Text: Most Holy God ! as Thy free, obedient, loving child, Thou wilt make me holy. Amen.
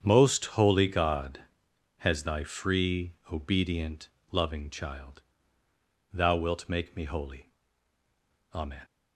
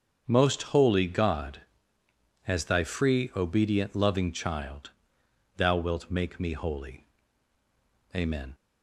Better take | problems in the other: second | starts louder than the rest; strong; until 1.1 s; 8 dB; strong in the second // says "has" for "as"; at 1.9 s

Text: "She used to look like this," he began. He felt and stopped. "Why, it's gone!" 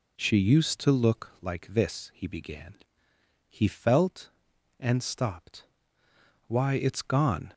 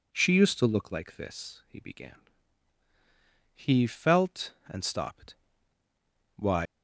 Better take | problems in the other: first | stops before "it's gone"; at 6.6 s

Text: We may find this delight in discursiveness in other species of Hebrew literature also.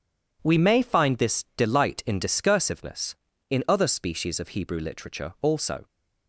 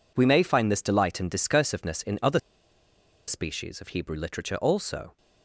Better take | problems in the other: first | pauses between "other" and "species"; noticeable; at 2.3 s; 0.88 s long

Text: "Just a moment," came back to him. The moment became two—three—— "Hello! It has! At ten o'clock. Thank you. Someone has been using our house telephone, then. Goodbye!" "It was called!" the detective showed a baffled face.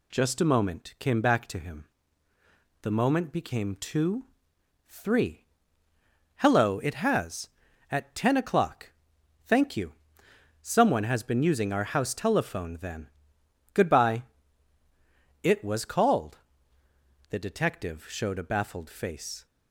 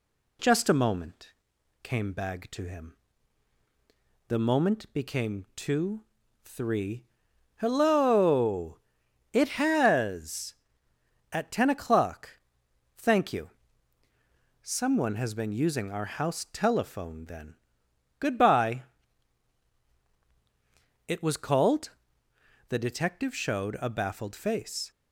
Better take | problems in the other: first | says "bag" for "back"; at 2.1 s

